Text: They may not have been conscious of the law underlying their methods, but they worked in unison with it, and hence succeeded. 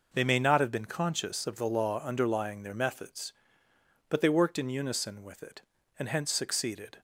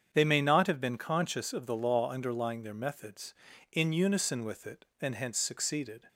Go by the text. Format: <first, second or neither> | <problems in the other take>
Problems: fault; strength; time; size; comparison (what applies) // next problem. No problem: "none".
first | starts louder than the rest; strong; until 1.1 s; 7.5 dB // skips "but they worked"; at 3.5 s